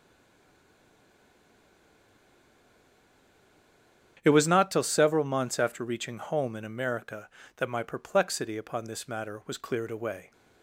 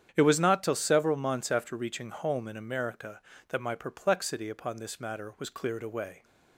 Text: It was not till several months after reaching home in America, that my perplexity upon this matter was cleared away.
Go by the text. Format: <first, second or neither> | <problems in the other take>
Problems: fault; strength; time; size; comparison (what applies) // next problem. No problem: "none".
second | stays silent before the first word; strong; until 4.1 s; 4.1 s long // starts louder than the rest; strong; until 5.2 s; 9 dB; strong in the second